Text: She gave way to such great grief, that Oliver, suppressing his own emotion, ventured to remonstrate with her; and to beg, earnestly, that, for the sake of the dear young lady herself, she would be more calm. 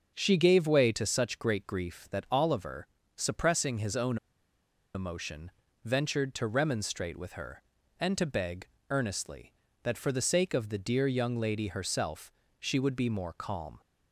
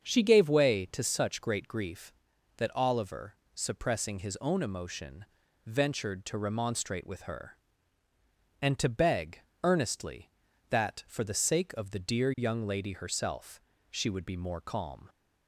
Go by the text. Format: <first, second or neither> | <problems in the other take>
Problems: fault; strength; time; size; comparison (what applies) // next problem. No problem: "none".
second | starts louder than the rest; until 1.1 s; 6.5 dB; strong in the second // pauses between "own" and "emotion"; noticeable; at 4.1 s; 0.78 s long